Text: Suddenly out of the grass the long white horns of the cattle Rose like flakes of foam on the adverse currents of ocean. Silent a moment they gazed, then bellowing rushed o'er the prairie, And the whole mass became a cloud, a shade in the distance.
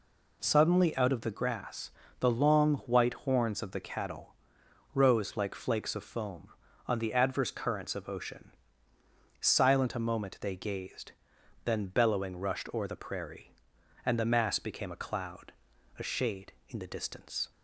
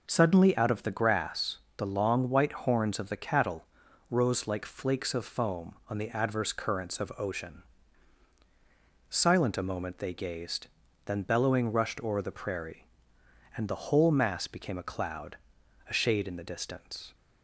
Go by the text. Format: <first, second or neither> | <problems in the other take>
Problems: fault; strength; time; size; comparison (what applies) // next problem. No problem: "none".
second | pauses between "grass" and "the"; slight; at 1.9 s; 0.28 s long; slight in the second // pauses between "cattle" and "Rose"; noticeable; at 4.3 s; 0.62 s long; also in the second // skips "whole"; at 14.2 s